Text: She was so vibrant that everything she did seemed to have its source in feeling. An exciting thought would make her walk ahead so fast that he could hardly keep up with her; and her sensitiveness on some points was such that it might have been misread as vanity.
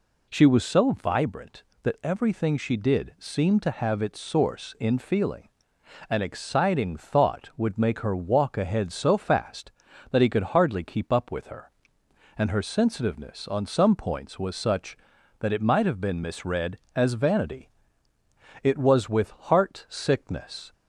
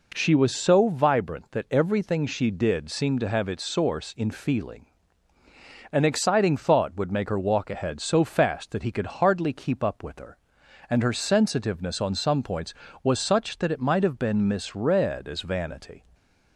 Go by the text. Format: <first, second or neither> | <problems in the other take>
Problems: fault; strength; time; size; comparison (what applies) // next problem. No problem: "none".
second | goes on to say "It was with heart sickness"; strong; from 18.6 s on; 2.1 s long